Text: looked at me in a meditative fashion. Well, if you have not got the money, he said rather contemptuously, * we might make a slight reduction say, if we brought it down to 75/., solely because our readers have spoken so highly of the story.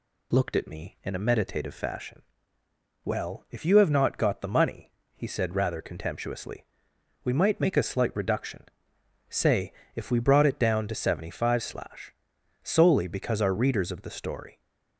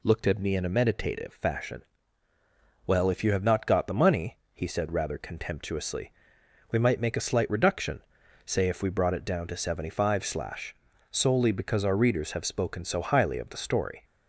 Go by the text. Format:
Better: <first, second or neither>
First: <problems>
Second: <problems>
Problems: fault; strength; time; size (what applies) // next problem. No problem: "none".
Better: second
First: pauses between "reduction" and "say"; noticeable; at 8.6 s; 0.70 s long // skips "have spoken so highly"; at 13.9 s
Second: pauses between "reduction" and "say"; noticeable; at 8.0 s; 0.48 s long